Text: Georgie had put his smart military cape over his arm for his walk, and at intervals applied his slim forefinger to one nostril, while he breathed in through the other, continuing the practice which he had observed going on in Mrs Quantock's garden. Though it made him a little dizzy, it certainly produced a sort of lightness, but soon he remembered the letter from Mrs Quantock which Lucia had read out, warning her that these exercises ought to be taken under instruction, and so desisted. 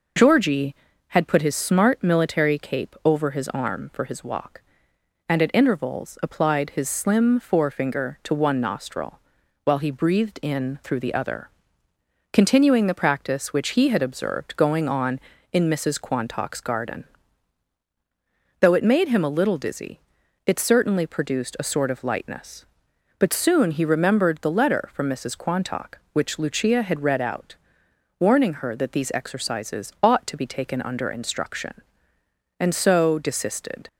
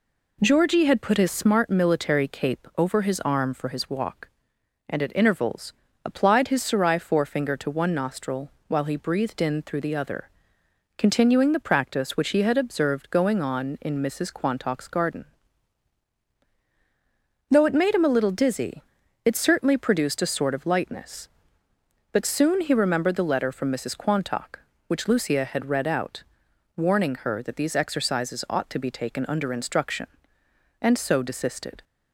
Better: first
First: none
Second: pauses between "intervals" and "applied"; slight; at 5.7 s; 0.32 s long // says "sarai" for "slim"; at 6.6 s

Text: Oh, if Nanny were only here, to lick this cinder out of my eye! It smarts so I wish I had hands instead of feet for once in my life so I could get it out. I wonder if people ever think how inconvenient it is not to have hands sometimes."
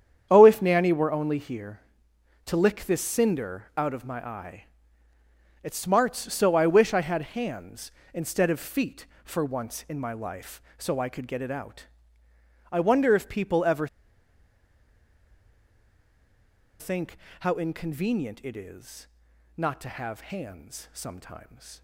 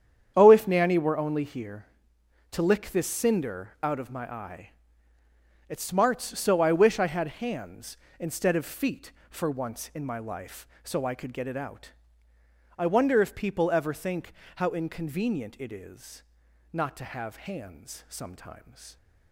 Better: second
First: starts louder than the rest; strong; until 1.3 s; 8.5 dB // pauses between "ever" and "think"; strong; at 13.8 s; 2.9 s long // pauses between "think" and "how"; slight; at 17.1 s; 0.24 s long // pauses between "is" and "not"; noticeable; at 19.0 s; 0.50 s long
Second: starts louder than the rest; strong; until 1.3 s; 8.5 dB // pauses between "think" and "how"; slight; at 14.3 s; 0.24 s long // pauses between "is" and "not"; noticeable; at 16.2 s; 0.50 s long

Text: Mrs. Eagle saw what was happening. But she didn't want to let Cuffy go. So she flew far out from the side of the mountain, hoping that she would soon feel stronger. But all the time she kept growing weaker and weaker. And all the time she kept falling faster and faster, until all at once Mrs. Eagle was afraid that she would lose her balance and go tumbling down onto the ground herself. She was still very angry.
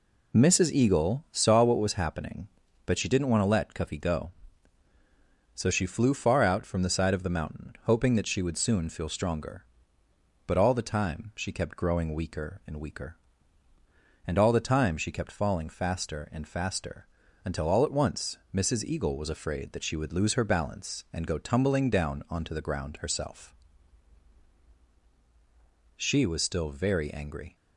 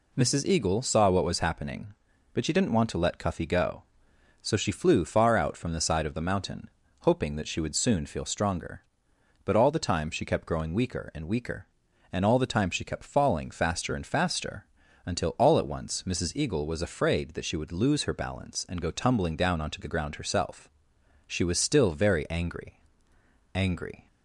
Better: first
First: none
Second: says "angry" twice; at 23.5 s

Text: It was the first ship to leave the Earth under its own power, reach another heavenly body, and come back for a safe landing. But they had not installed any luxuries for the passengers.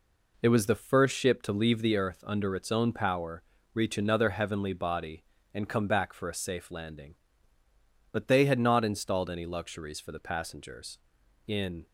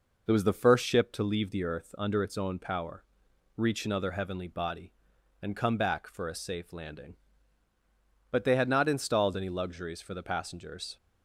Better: second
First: goes on to say "In"; slight; from 11.4 s on; 0.40 s long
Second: none

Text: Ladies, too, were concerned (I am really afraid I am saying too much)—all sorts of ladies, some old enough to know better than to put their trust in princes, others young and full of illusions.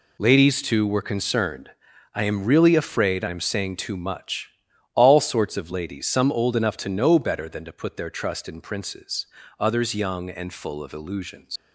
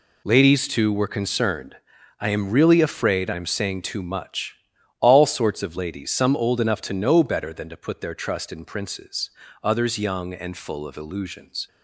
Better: second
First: leaves "illusions" unfinished; at 11.5 s; 70 ms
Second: none

